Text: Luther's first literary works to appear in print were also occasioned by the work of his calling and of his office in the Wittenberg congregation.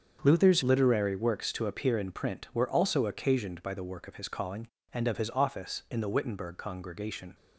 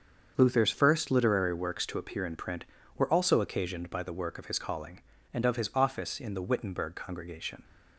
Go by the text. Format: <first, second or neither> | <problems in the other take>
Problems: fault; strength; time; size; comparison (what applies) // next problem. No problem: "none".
second | starts louder than the rest; until 1.2 s; 7 dB; also in the second // skips "first"; at 0.6 s